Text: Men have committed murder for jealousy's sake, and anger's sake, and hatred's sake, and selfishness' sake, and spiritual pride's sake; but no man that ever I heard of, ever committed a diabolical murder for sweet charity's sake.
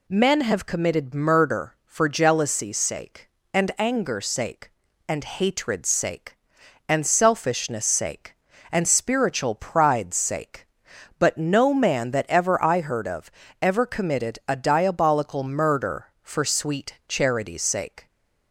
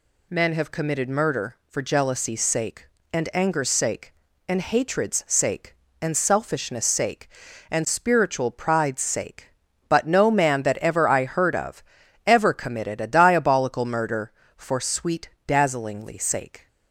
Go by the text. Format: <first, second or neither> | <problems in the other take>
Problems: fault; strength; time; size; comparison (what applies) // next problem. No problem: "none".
first | says "dazzlingly" for "charity's"; at 15.4 s